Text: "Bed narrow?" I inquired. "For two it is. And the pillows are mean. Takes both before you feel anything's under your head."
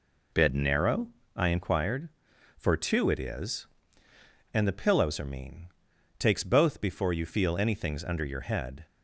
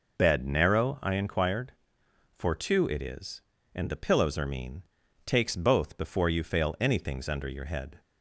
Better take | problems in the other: first | says "fail" for "feel"; at 6.4 s

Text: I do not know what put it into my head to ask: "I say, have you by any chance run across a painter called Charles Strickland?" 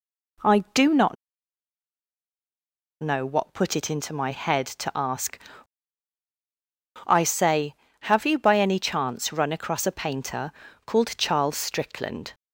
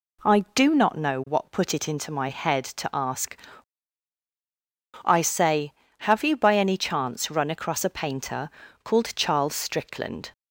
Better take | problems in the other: second | pauses between "not" and "know"; strong; at 1.1 s; 1.8 s long // pauses between "painter" and "called"; slight; at 10.4 s; 0.36 s long; slight in the second

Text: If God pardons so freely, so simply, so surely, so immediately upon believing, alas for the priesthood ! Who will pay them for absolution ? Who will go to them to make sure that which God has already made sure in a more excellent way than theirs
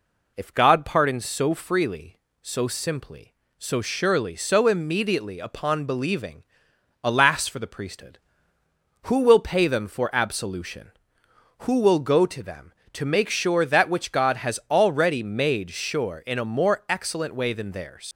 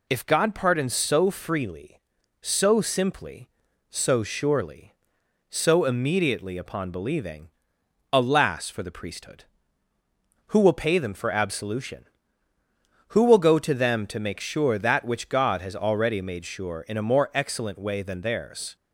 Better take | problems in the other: second | leaves "theirs" unfinished; at 18.1 s; 105 ms

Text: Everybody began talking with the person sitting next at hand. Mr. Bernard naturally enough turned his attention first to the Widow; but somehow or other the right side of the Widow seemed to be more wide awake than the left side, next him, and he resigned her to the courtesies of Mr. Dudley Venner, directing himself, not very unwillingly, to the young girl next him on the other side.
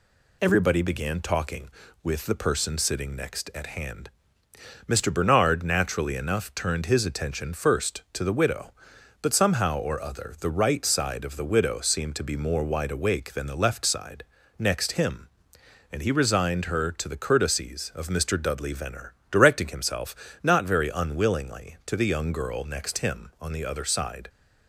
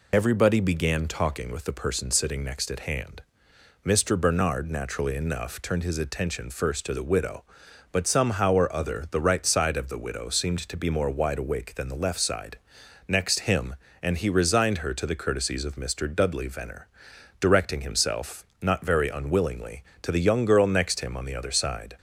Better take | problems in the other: first | loses the start of "Everybody"; at 0.1 s; 40 ms

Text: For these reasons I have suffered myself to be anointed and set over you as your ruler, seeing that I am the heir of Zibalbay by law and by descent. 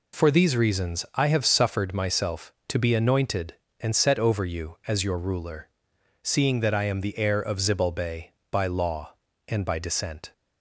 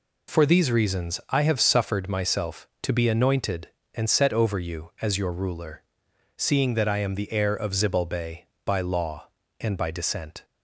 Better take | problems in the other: neither | none

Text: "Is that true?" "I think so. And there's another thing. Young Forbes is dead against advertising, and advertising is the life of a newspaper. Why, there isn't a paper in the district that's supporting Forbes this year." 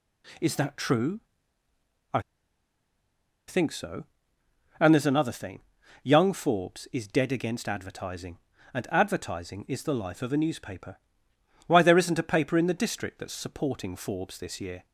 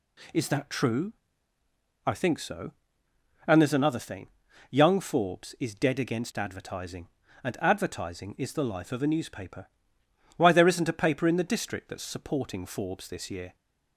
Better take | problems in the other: second | pauses between "I" and "think"; strong; at 2.1 s; 1.2 s long

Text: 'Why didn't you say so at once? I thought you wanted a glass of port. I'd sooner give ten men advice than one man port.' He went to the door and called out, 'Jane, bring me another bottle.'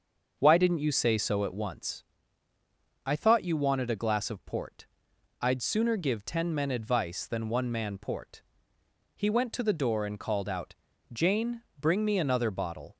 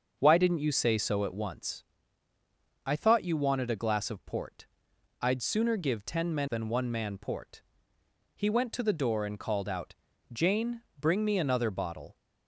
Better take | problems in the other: first | starts louder than the rest; until 1.2 s; 6.5 dB; also in the first // skips "advice"; at 6.4 s

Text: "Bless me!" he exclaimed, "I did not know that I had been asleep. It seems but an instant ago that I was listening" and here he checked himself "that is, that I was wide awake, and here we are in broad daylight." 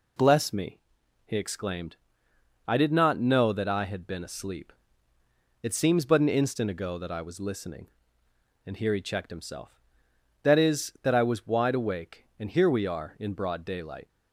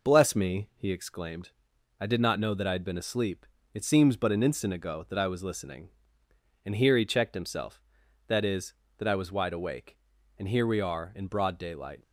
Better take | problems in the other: neither | none

